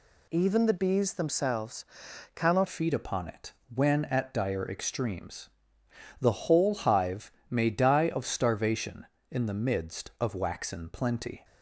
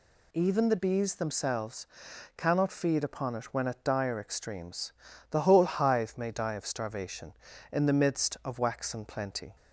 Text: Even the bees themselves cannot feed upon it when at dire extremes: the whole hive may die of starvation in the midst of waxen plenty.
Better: second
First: pauses between "themselves" and "cannot"; noticeable; at 1.8 s; 0.50 s long // changes voice at "feed"; from 2.6 s on; 8.8 s long // pauses between "it" and "when"; slight; at 3.5 s; 0.22 s long // pauses between "hive" and "may"; slight; at 7.3 s; 0.20 s long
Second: pauses between "themselves" and "cannot"; noticeable; at 1.8 s; 0.50 s long

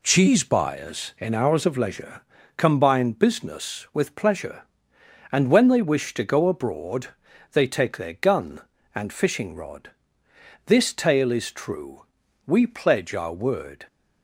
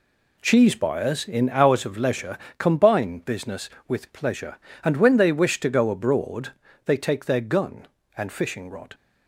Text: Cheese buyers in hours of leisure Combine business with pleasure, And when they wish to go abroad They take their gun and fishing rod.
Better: second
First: pauses between "leisure" and "Combine"; slight; at 2.2 s; 0.34 s long // pauses between "abroad" and "They"; noticeable; at 7.0 s; 0.46 s long // goes on to say "This tale is true we pledge our word"; strong; from 10.6 s on; 3.2 s long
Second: pauses between "leisure" and "Combine"; slight; at 2.3 s; 0.20 s long // pauses between "abroad" and "They"; slight; at 6.5 s; 0.32 s long

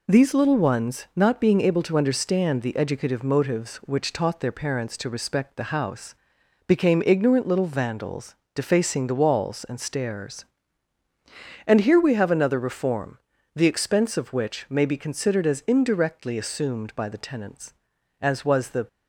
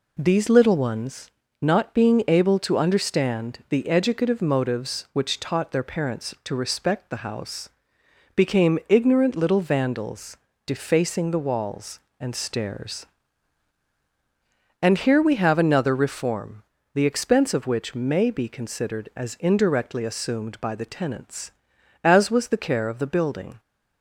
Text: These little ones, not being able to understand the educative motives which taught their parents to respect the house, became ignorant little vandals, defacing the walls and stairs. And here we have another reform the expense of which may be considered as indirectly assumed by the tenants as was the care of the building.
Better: second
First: pauses between "reform" and "the"; at 13.1 s; 0.38 s long // stops before "care of the building"; at 18.8 s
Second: pauses between "reform" and "the"; slight; at 16.6 s; 0.30 s long

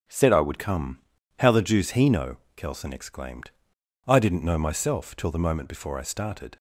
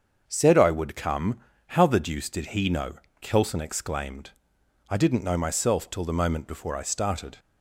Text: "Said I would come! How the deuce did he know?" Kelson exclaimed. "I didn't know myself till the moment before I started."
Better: second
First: starts louder than the rest; strong; until 1.4 s; 8.5 dB // skips "did"; at 1.9 s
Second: starts louder than the rest; until 1.2 s; 7 dB

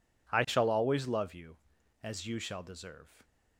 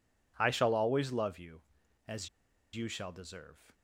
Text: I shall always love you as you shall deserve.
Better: first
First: none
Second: pauses between "as" and "you"; at 2.2 s; 0.44 s long

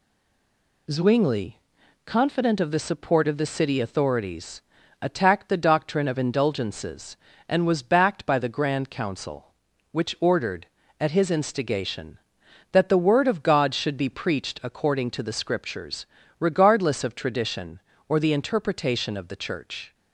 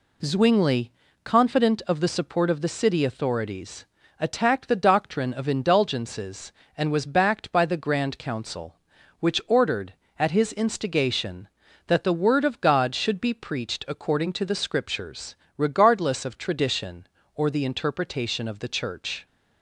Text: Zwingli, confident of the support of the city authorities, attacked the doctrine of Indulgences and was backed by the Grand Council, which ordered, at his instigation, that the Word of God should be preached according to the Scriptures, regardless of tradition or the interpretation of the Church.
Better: second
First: stays silent before the first word; slight; until 0.8 s; 0.8 s long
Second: none

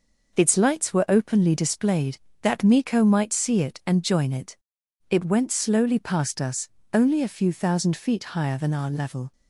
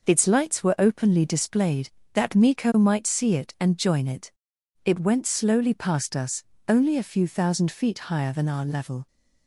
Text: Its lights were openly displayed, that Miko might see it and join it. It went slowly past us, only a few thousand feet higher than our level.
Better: neither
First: none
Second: none

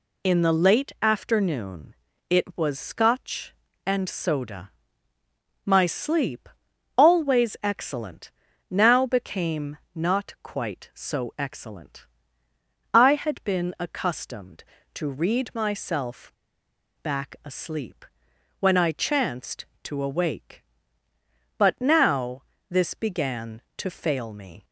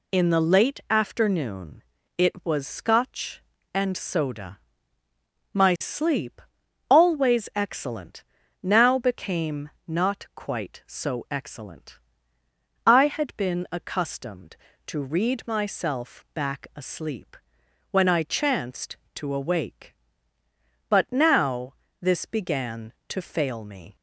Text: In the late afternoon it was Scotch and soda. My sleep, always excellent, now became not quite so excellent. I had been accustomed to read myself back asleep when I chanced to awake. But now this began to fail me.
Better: second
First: pauses between "afternoon" and "it"; slight; at 1.9 s; 0.34 s long // pauses between "became" and "not"; slight; at 9.7 s; 0.18 s long // pauses between "myself" and "back"; noticeable; at 16.3 s; 0.69 s long // pauses between "asleep" and "when"; noticeable; at 18.0 s; 0.54 s long // pauses between "now" and "this"; slight; at 22.4 s; 0.28 s long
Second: pauses between "afternoon" and "it"; slight; at 1.8 s; 0.34 s long // pauses between "became" and "not"; slight; at 9.6 s; 0.18 s long // pauses between "asleep" and "when"; noticeable; at 17.3 s; 0.54 s long // pauses between "now" and "this"; slight; at 21.7 s; 0.28 s long

